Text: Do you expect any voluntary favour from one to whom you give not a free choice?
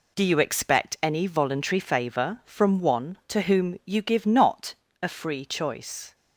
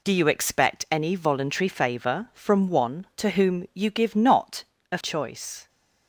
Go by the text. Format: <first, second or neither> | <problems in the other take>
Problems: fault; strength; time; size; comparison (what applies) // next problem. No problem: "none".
first | pauses between "not" and "a"; slight; at 4.6 s; 0.30 s long; slight in the first // skips "free"; at 4.9 s